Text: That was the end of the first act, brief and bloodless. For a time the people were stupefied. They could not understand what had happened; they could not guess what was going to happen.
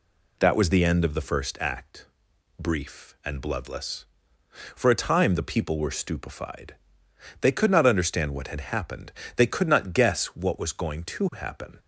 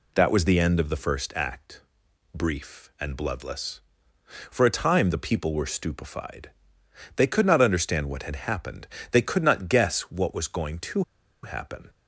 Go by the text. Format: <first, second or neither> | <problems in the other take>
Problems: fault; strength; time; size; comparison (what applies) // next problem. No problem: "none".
first | pauses between "to" and "happen"; at 11.0 s; 0.39 s long